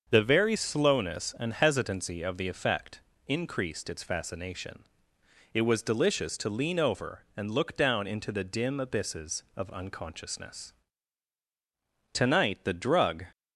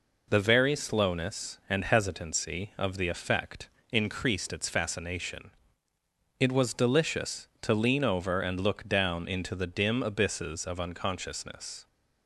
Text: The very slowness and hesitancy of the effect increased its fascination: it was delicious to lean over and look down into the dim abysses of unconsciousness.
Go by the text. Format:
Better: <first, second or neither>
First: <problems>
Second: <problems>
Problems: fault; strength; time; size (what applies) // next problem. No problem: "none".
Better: second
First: starts louder than the rest; until 1.0 s; 6.5 dB // pauses between "effect" and "increased"; slight; at 3.0 s; 0.26 s long // goes on to say "Tonight the drug"; noticeable; from 12.1 s on; 1.1 s long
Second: pauses between "effect" and "increased"; slight; at 3.6 s; 0.22 s long